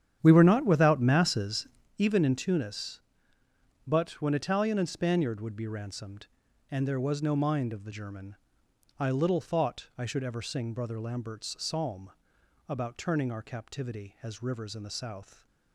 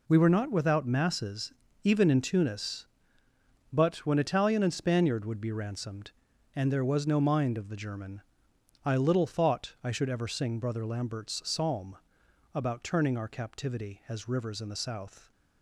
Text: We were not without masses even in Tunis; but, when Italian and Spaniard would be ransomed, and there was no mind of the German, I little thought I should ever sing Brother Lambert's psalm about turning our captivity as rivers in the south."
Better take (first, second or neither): second